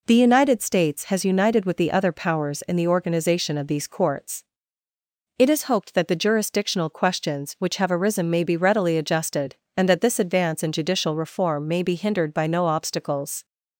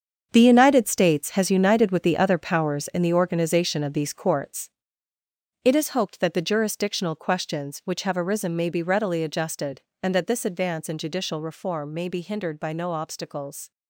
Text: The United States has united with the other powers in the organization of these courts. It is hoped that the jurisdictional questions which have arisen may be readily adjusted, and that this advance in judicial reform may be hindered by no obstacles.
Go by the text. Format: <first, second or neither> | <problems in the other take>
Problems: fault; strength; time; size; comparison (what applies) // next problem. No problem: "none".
first | gets quieter; strong; throughout; 10 dB